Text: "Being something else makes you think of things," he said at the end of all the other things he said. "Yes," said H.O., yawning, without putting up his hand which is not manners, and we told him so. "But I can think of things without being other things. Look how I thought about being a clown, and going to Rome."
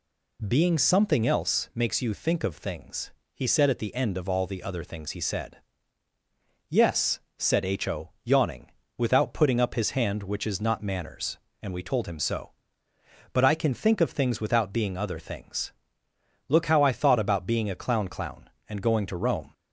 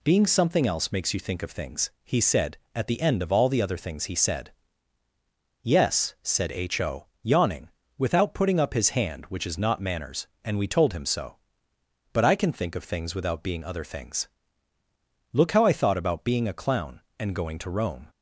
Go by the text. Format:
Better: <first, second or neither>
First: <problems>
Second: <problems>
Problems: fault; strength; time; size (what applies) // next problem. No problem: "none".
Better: second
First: says "clown" twice; at 18.0 s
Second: none